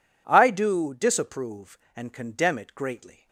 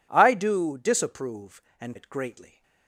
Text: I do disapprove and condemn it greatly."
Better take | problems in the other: first | skips "condemn"; at 1.9 s

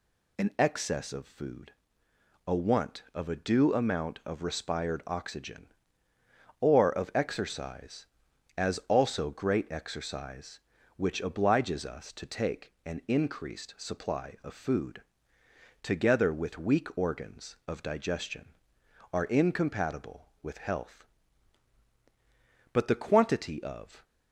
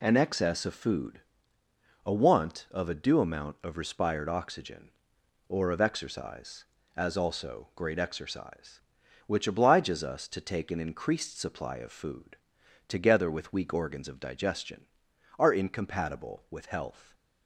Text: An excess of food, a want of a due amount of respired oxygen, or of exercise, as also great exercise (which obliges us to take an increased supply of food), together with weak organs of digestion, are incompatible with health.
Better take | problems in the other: second | goes on to say "But the quantity of"; noticeable; from 22.7 s on; 1.3 s long

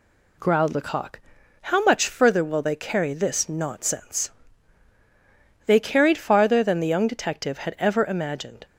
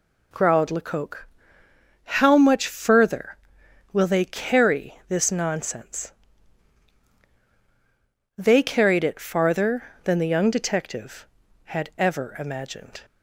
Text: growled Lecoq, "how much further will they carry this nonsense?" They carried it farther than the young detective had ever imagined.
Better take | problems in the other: second | skips "it"; at 6.1 s

